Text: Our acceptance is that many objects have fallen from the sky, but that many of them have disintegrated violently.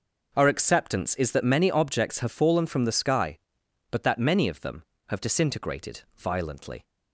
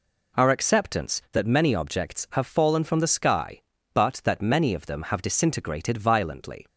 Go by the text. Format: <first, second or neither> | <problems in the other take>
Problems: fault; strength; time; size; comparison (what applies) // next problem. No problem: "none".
first | skips "is"; at 1.2 s